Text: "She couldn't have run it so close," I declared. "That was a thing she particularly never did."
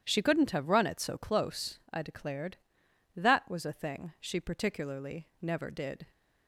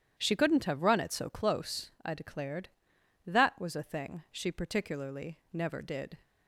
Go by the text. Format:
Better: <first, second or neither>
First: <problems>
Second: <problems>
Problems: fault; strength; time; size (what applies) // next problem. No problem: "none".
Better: neither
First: starts louder than the rest; strong; until 1.0 s; 10 dB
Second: starts louder than the rest; strong; until 1.2 s; 10 dB